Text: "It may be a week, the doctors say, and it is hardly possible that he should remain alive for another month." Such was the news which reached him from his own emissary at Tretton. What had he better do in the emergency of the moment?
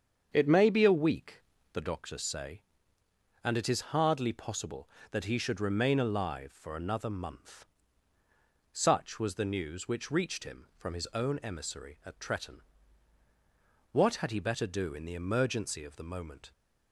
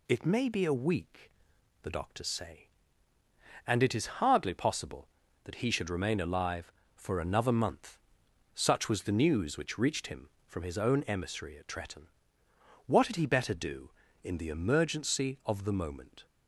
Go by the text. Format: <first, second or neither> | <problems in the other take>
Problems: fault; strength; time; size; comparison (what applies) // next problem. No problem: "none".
second | starts louder than the rest; strong; until 1.8 s; 7.5 dB